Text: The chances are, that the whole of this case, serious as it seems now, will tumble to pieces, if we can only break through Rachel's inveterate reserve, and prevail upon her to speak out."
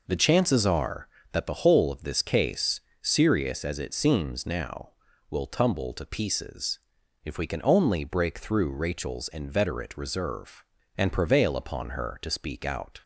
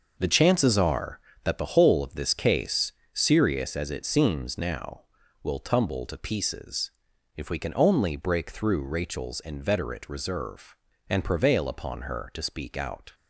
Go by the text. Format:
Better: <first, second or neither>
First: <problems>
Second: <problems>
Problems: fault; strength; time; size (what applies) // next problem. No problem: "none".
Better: first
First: none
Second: gets quieter; strong; throughout; 9 dB